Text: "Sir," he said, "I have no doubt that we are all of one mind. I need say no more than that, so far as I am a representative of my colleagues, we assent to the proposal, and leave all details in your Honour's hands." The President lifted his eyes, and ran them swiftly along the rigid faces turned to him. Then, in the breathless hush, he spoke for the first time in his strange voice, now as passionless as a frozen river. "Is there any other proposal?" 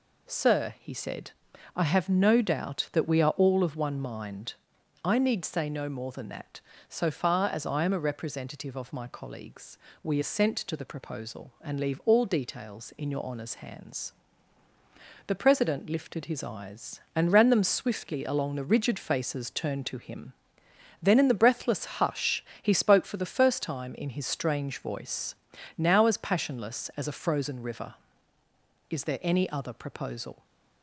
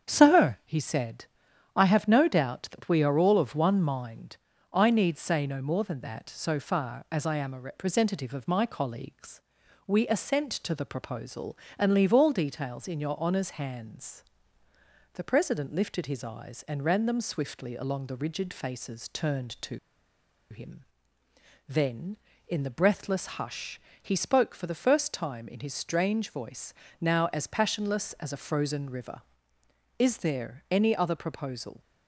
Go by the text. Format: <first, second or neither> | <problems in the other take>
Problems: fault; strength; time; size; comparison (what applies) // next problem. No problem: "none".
first | starts louder than the rest; strong; until 1.1 s; 8 dB // pauses between "to" and "him"; noticeable; at 19.7 s; 0.72 s long